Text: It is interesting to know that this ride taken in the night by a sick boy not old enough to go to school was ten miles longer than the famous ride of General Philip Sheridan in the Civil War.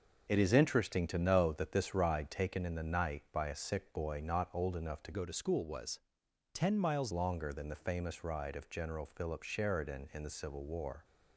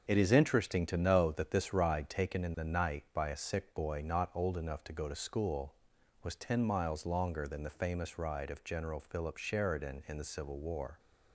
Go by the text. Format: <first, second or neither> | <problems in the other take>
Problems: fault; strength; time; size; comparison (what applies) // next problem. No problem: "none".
second | starts louder than the rest; until 1.3 s; 6.5 dB; also in the second // changes voice from "go" to "miles"; from 5.1 to 7.1 s; 2.0 s long // pauses between "was" and "ten"; noticeable; at 5.9 s; 0.56 s long